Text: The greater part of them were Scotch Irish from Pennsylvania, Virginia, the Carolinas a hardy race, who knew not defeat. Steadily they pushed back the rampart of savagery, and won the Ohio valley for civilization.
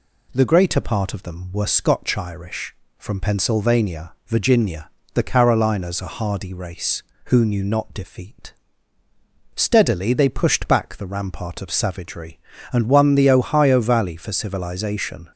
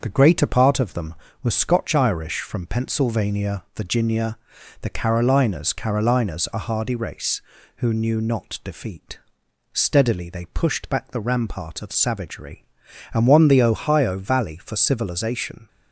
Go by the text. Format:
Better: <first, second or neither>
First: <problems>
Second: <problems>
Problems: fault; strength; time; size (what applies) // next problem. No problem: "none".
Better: first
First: none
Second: starts louder than the rest; until 1.0 s; 6 dB // says "Carolinas" twice; at 5.7 s